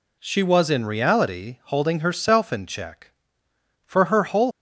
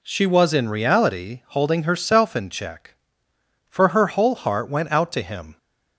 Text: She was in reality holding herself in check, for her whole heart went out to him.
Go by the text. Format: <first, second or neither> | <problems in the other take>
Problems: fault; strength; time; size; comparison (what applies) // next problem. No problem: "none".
second | stops before "heart went out to him"; at 4.5 s